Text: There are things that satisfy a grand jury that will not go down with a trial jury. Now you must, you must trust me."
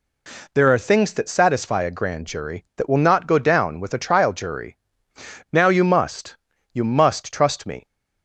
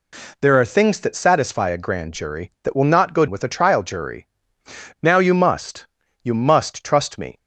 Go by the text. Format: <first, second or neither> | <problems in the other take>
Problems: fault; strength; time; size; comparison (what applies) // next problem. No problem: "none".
first | skips "down"; at 3.2 s